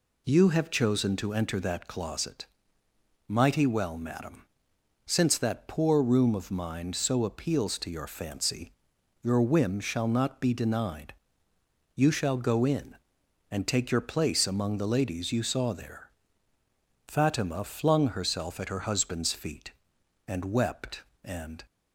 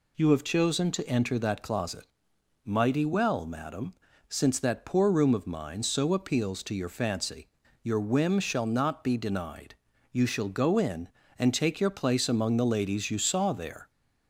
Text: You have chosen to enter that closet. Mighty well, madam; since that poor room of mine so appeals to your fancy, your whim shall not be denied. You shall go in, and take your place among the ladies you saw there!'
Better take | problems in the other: second | goes on to say "Fatima flung herself at her husband's feet and wept and"; strong; from 17.0 s on; 4.5 s long

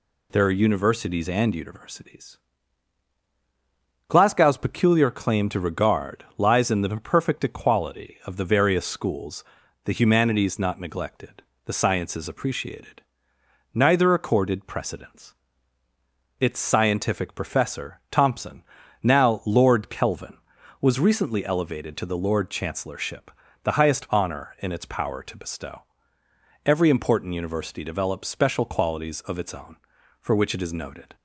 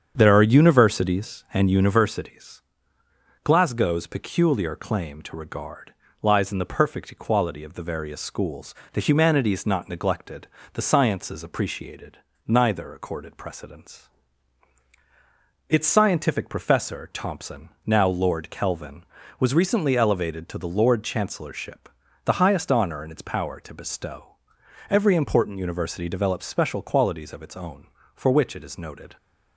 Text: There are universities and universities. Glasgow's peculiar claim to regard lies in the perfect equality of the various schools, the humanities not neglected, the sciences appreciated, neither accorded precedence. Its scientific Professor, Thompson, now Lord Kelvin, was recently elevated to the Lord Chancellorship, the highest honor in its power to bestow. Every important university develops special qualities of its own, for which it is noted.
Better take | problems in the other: first | starts louder than the rest; strong; until 1.7 s; 8 dB // pauses between "regard" and "lies"; slight; at 5.9 s; 0.30 s long

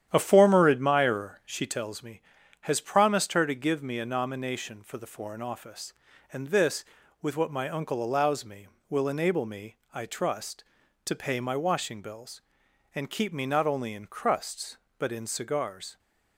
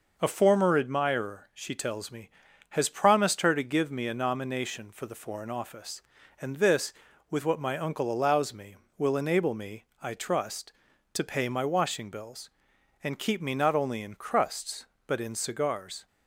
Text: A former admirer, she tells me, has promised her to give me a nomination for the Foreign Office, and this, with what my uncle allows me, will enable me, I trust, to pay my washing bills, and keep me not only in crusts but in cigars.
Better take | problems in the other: second | starts louder than the rest; strong; until 1.8 s; 10 dB

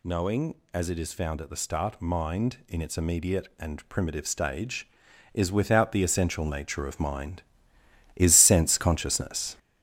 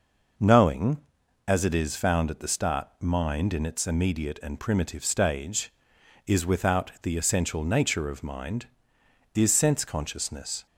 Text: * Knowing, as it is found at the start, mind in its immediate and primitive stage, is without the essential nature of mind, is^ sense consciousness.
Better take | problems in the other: second | gets louder; throughout; 6.5 dB

